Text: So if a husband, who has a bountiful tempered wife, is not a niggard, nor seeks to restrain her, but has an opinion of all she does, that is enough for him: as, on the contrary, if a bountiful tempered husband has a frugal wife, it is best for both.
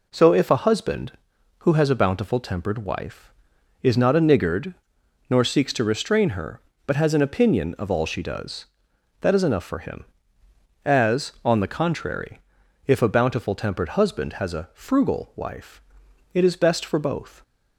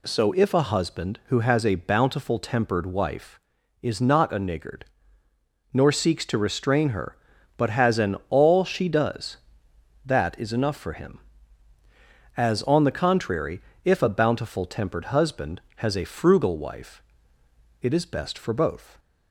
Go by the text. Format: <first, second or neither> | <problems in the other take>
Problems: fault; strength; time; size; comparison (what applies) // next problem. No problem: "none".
first | skips "opinion of"; at 8.2 s